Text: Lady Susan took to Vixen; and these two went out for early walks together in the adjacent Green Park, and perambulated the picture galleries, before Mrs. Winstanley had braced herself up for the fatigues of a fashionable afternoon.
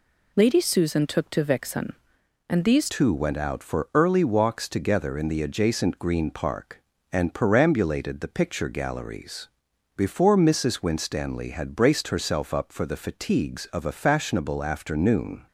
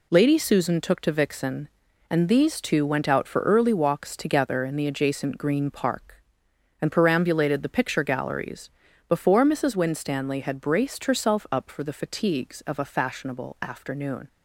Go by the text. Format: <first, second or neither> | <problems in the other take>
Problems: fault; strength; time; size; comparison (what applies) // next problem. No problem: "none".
second | changes voice at "two"; from 2.8 s on; 12.6 s long